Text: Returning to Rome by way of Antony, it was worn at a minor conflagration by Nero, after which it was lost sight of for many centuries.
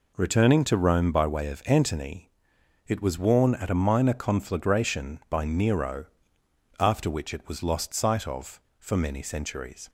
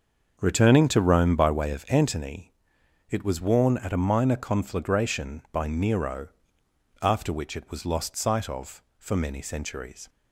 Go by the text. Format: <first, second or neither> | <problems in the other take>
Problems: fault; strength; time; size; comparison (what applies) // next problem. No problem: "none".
first | starts louder than the rest; until 2.0 s; 6.5 dB